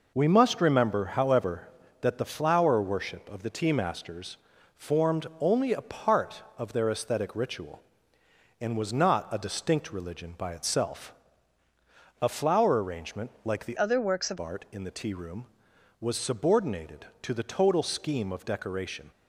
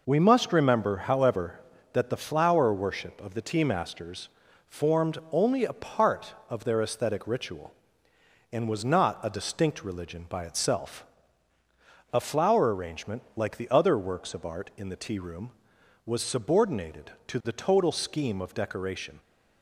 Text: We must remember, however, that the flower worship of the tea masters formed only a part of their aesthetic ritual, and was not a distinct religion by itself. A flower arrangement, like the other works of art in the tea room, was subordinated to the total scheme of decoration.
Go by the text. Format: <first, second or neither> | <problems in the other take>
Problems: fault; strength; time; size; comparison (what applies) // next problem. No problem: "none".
second | pauses between "masters" and "formed"; at 4.3 s; 0.40 s long; also in the second // changes voice from "other" to "of"; from 13.7 to 14.3 s; 0.6 s long